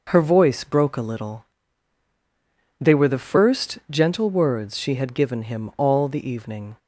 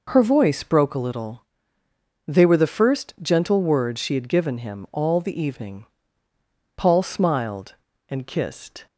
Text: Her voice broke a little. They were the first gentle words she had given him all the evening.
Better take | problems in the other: first | goes on to say "Paul smiled and kissed"; strong; from 6.7 s on; 2.1 s long

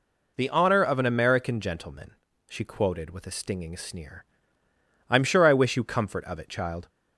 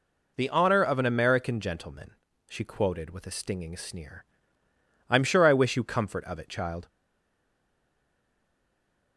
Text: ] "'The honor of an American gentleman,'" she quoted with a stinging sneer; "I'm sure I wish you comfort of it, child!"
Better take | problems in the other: first | stays silent after the last word; from 6.8 s on; 2.3 s long

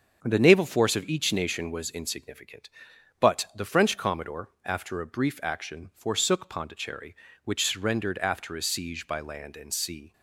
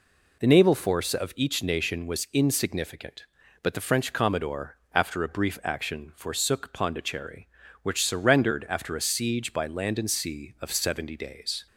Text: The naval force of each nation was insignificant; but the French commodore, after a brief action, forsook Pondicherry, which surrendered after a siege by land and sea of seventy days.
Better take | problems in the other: second | starts louder than the rest; until 1.2 s; 7 dB // stops before "of seventy days"; at 10.1 s

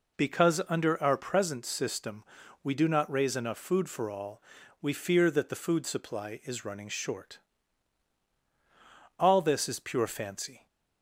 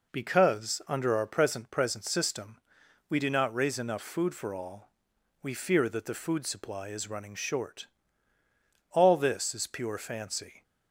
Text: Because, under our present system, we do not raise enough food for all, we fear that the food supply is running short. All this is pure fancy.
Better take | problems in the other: first | says "present" twice; at 1.6 s

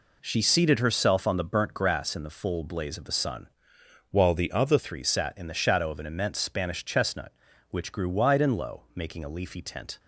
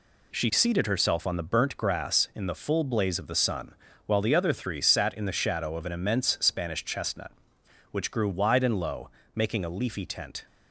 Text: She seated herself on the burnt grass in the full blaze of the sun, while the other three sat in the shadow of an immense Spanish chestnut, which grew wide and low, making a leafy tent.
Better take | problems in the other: second | changes voice from "while" to "other"; from 4.1 to 4.7 s; 0.6 s long

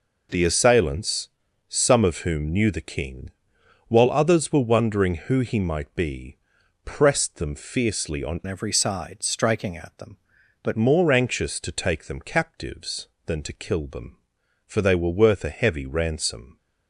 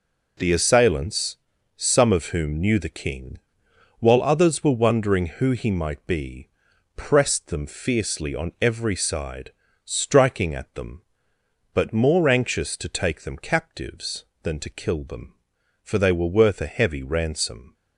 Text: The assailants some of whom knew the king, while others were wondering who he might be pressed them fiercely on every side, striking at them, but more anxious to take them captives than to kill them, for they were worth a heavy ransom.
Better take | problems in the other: second | pauses between "assailants" and "some"; at 1.2 s; 0.44 s long; also in the second // pauses between "be" and "pressed"; noticeable; at 6.3 s; 0.48 s long; noticeable in the second // changes voice from "every" to "but"; from 8.4 to 10.7 s; 2.3 s long

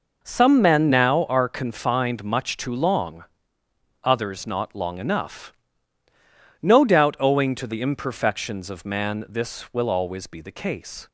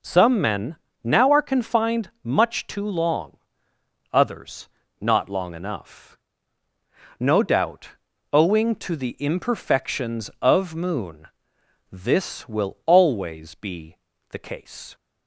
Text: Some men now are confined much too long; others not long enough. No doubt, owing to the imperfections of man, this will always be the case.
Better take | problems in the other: first | pauses between "men" and "now"; slight; at 0.7 s; 0.26 s long // pauses between "others" and "not"; slight; at 4.6 s; 0.32 s long // says "moon" for "man"; at 10.7 s // pauses between "be" and "the"; slight; at 13.9 s; 0.32 s long

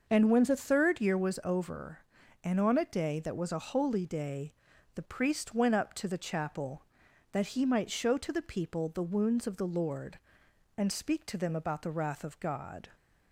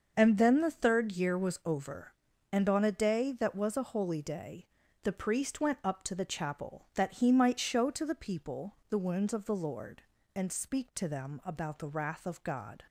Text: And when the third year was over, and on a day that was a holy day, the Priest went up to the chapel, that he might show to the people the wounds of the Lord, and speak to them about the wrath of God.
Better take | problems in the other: first | starts louder than the rest; until 1.1 s; 6.5 dB; noticeable in the first // says "then" for "when"; at 0.3 s

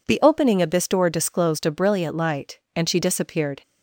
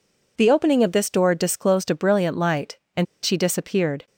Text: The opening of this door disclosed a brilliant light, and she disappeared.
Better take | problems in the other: first | pauses between "and" and "she"; slight; at 3.0 s; 0.18 s long

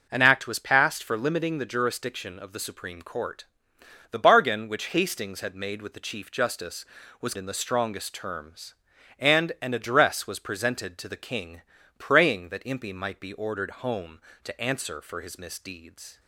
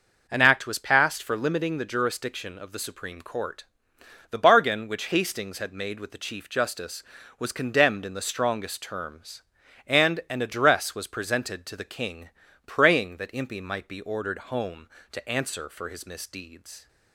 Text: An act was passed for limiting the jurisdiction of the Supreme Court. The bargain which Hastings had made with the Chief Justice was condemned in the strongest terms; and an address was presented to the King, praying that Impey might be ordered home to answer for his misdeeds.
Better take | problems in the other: second | skips "condemned"; at 7.3 s

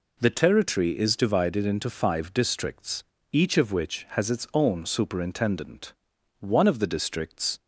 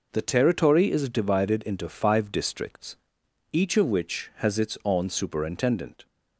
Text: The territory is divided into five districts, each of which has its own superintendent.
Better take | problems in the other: second | goes on to say "One of the districts"; noticeable; from 6.3 s on; 1.2 s long

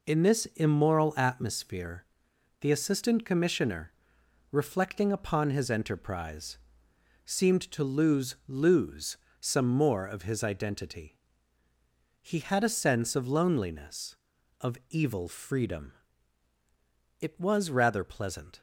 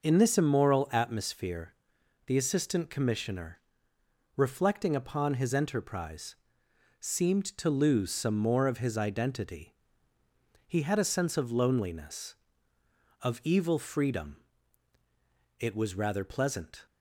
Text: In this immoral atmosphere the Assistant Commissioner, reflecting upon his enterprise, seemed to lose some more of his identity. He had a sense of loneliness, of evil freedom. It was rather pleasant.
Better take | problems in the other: second | pauses between "atmosphere" and "the"; noticeable; at 2.0 s; 0.56 s long; noticeable in the second // says "lose" twice; at 8.4 s

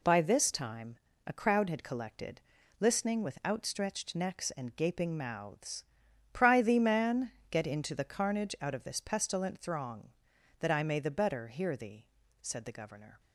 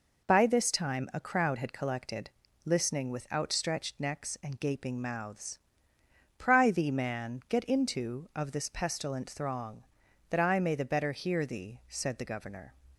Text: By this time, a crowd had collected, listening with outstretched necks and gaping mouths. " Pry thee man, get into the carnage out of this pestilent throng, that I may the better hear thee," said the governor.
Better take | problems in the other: first | skips "the carnage out"; at 8.3 s

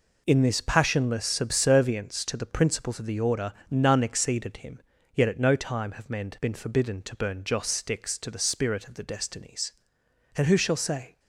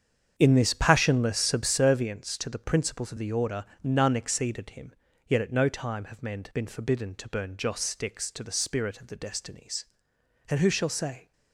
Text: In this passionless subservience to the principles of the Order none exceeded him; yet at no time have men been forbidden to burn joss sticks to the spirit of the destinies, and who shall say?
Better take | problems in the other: first | starts louder than the rest; strong; until 1.7 s; 7.5 dB // pauses between "Order" and "none"; slight; at 3.6 s; 0.18 s long; slight in the first

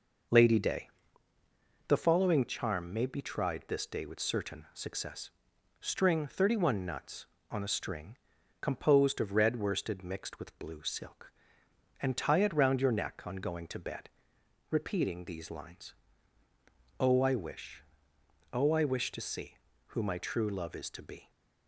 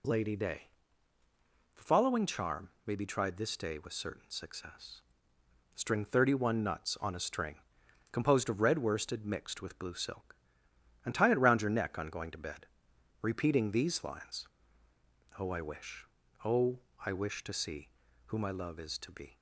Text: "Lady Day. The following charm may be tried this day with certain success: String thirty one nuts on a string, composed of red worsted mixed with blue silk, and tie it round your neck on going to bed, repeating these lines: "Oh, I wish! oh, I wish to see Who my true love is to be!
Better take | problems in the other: first | pauses between "charm" and "may"; slight; at 2.6 s; 0.16 s long // skips "true"; at 18.5 s

